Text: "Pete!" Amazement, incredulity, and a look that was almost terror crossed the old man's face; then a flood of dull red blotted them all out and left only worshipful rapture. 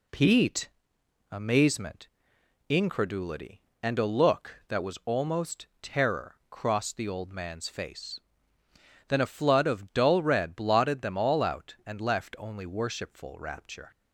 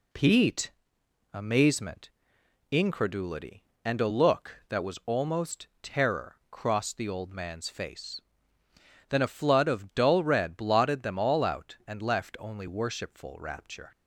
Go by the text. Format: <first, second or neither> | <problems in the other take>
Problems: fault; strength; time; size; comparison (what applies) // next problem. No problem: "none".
neither | pauses between "almost" and "terror"; slight; the same in both